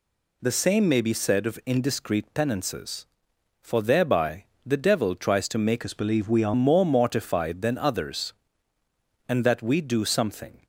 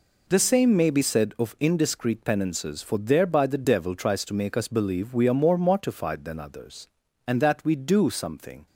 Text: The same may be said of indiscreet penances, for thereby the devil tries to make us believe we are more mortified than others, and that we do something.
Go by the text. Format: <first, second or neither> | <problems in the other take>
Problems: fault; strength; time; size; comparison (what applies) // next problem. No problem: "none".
second | pauses between "thereby" and "the"; slight; at 4.4 s; 0.22 s long // changes voice from "us" to "are"; from 5.8 to 6.5 s; 0.7 s long